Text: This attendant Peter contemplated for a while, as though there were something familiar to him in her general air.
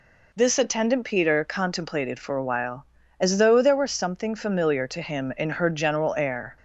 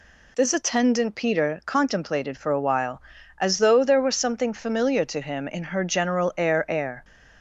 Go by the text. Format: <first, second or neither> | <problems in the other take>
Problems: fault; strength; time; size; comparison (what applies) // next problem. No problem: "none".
first | says "air" twice; at 6.7 s